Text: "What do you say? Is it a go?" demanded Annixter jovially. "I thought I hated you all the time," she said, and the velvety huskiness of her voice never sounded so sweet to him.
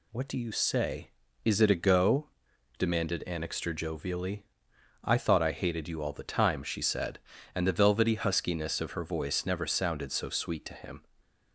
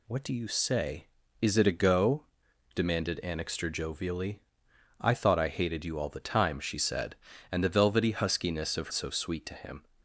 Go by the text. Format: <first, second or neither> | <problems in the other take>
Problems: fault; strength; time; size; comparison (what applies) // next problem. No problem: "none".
first | skips "her voice never sounded"; at 8.9 s